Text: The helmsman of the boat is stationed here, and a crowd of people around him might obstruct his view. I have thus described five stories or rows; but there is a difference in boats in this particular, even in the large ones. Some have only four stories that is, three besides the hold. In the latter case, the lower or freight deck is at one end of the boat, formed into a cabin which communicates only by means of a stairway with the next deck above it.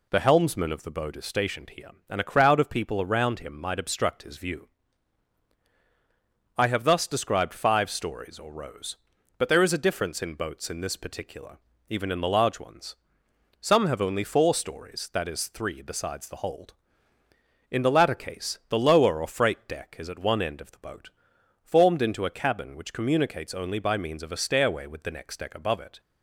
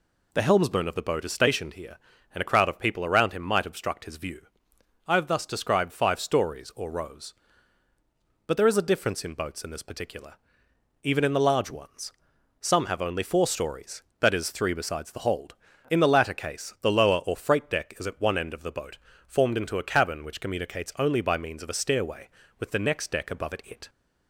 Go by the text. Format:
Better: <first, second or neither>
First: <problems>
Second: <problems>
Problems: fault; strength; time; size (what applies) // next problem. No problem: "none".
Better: first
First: none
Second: says "it" twice; at 23.6 s